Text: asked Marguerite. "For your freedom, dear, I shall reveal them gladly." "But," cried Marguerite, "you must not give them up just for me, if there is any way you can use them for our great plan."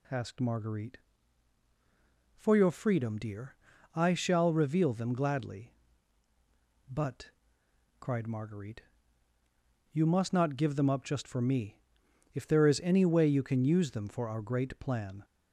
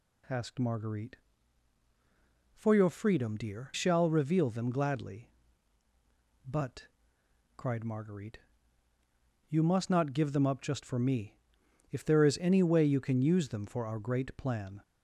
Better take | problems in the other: first | skips "I"; at 3.7 s

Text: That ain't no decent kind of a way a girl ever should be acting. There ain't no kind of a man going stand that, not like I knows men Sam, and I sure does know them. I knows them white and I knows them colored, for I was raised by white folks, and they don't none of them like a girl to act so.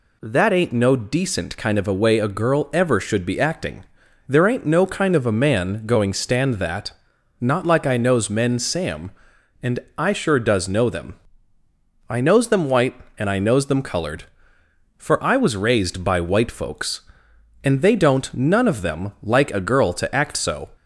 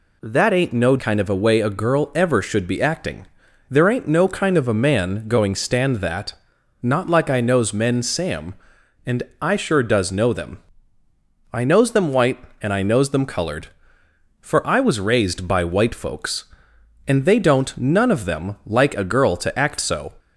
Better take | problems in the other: first | skips "decent"; at 0.9 s // pauses between "and" and "I"; slight; at 9.2 s; 0.18 s long; slight in the first

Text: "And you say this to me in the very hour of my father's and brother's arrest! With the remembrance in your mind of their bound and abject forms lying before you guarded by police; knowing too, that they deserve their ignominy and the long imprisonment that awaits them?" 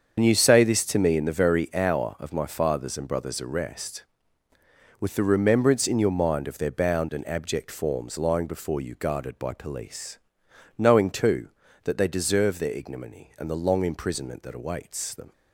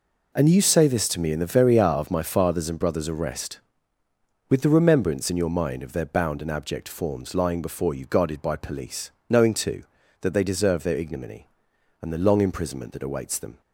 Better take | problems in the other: second | loses the start of "And"; at 0.1 s; 70 ms // starts louder than the rest; until 1.2 s; 7 dB

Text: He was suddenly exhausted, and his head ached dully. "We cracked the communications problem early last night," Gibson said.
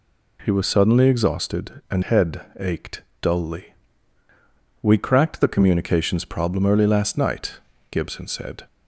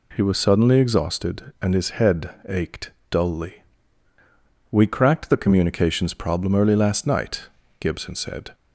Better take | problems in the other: second | skips "his"; at 2.0 s // pauses between "head" and "ached"; slight; at 2.3 s; 0.18 s long; slight in the second // pauses between "ached" and "dully"; slight; at 3.0 s; 0.18 s long; slight in the second

